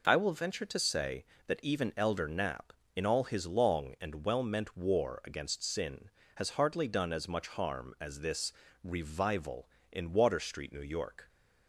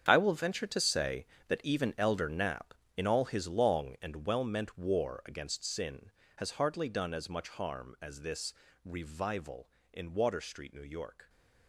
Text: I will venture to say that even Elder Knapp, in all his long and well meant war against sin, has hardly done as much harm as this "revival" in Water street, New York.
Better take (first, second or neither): first